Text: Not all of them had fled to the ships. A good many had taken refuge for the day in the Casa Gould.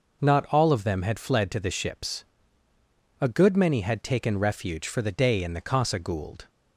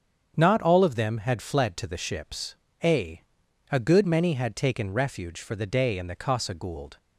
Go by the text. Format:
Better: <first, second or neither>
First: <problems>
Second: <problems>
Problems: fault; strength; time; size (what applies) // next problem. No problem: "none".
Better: first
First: none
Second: starts louder than the rest; strong; until 1.3 s; 7.5 dB // says "A" twice; at 3.7 s